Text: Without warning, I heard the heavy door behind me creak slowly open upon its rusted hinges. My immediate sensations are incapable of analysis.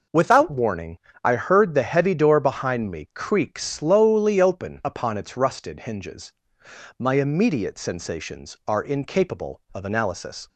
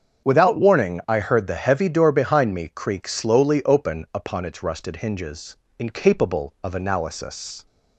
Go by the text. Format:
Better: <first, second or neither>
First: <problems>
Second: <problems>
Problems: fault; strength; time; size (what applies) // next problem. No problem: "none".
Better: first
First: none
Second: starts louder than the rest; until 1.3 s; 7 dB // skips "My immediate sensations are"; at 5.6 s